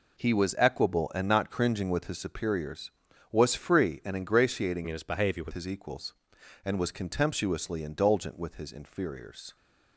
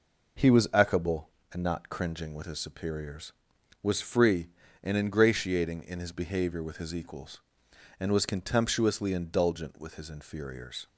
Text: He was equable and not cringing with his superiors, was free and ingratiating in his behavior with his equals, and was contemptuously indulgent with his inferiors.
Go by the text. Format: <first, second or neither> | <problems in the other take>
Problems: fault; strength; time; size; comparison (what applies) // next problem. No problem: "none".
second | changes voice from "in" to "with"; from 4.8 to 5.5 s; 0.7 s long